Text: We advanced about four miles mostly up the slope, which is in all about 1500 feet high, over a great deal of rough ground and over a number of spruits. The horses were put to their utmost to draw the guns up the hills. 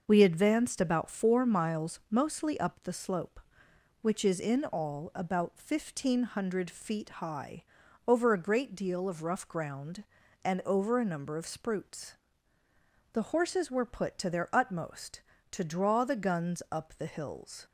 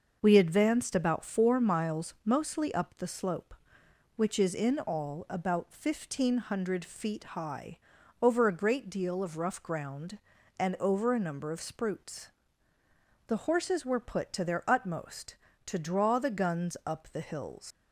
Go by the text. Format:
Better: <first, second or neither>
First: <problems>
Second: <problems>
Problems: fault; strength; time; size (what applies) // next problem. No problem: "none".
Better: first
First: none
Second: leaves "hills" unfinished; at 17.7 s; 90 ms